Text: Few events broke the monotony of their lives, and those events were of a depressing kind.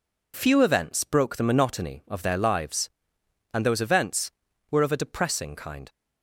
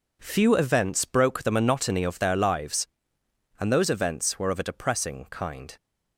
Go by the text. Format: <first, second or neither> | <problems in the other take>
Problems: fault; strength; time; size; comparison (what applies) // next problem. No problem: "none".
neither | none